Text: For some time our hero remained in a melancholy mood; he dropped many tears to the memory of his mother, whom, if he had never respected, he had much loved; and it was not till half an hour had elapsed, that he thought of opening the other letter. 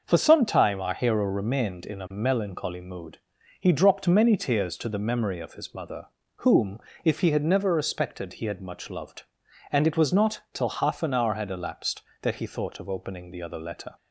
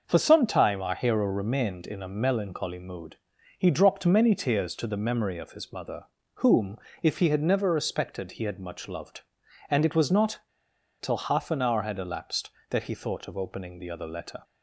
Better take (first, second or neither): first